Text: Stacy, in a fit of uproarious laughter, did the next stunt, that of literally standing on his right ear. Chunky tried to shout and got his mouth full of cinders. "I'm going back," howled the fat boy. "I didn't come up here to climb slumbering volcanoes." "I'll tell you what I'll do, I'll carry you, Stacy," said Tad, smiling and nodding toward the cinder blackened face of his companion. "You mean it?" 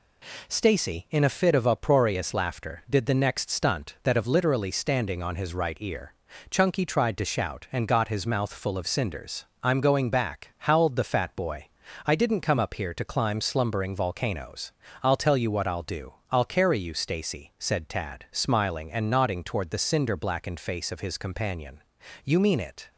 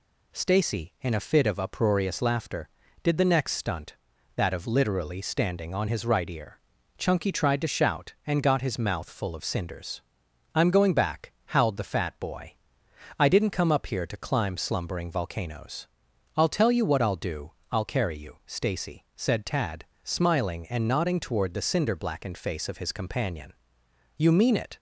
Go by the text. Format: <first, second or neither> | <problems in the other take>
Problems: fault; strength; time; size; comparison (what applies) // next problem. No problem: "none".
neither | none